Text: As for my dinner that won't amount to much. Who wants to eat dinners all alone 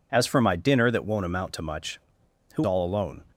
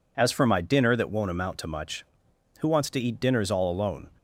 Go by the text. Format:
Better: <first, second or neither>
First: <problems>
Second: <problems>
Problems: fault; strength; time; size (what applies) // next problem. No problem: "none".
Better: second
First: skips "wants to eat dinners"; at 2.6 s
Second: none